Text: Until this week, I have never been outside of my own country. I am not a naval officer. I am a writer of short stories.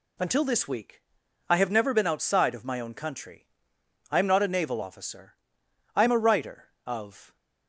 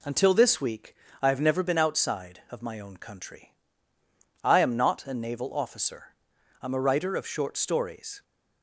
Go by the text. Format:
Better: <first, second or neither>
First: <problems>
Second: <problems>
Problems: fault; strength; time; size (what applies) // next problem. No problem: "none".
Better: second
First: stops before "short stories"; at 7.3 s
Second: none